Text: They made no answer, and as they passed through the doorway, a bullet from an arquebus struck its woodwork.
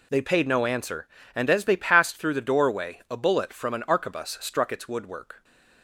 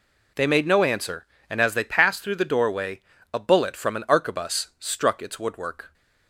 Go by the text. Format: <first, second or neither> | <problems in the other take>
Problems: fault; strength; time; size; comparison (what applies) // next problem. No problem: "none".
second | says "paid" for "made"; at 0.2 s